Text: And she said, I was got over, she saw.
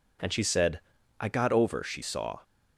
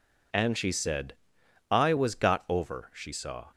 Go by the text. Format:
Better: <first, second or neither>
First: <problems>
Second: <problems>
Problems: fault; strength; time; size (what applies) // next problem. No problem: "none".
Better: second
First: skips "was"; at 1.2 s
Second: none